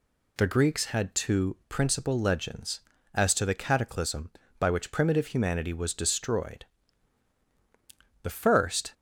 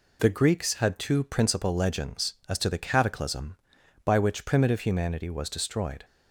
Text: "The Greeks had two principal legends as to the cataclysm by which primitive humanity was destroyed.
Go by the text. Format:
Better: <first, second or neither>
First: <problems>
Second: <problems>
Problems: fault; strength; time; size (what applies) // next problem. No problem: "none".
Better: second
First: goes on to say "The first"; noticeable; from 8.2 s on; 0.70 s long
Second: none